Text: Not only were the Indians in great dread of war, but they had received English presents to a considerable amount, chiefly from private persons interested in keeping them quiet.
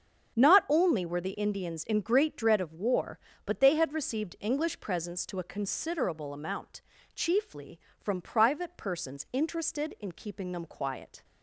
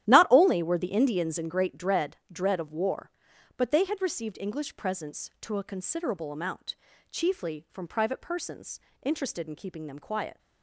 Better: first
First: starts louder than the rest; strong; until 1.4 s; 7.5 dB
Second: starts louder than the rest; strong; until 1.1 s; 12 dB // says "dread" twice; at 2.3 s // pauses between "persons" and "interested"; slight; at 8.7 s; 0.22 s long

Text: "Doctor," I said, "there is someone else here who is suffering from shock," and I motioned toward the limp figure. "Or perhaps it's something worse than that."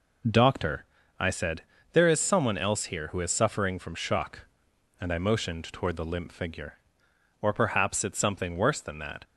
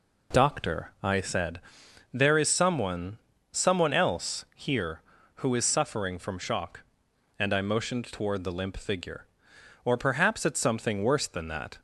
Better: first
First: none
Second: says "someone" twice; at 3.5 s

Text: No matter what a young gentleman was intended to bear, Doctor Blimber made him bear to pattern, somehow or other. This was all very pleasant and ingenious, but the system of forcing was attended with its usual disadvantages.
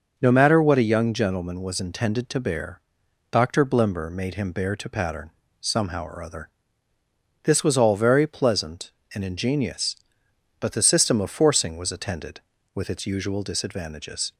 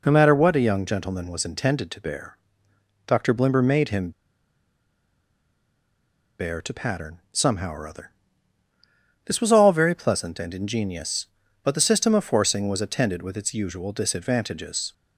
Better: first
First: none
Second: pauses between "him" and "bear"; strong; at 4.1 s; 2.2 s long

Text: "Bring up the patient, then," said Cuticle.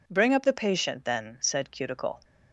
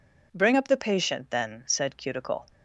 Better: neither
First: none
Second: none

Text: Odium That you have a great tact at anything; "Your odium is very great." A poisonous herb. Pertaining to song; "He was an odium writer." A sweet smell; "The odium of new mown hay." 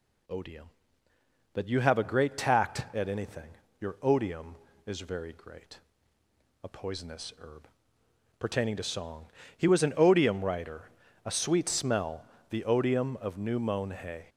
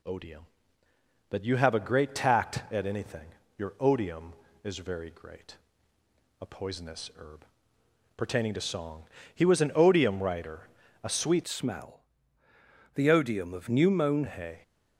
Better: first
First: none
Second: changes voice from "smell" to "mown"; from 11.4 to 14.2 s; 2.8 s long

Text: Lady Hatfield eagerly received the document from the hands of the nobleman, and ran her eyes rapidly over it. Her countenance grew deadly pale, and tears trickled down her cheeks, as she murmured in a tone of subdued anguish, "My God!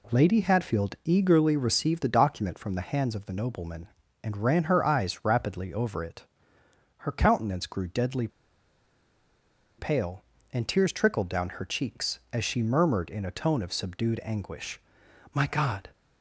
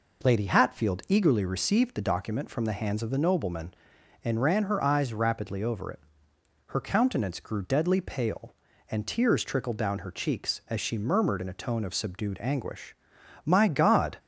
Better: second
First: pauses between "deadly" and "pale"; strong; at 8.2 s; 1.5 s long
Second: none

